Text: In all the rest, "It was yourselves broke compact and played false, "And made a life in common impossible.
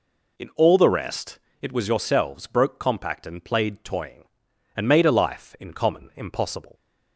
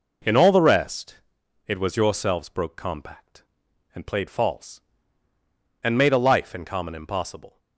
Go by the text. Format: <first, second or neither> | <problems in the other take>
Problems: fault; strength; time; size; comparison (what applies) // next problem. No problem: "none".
second | says "toying" for "false"; at 3.8 s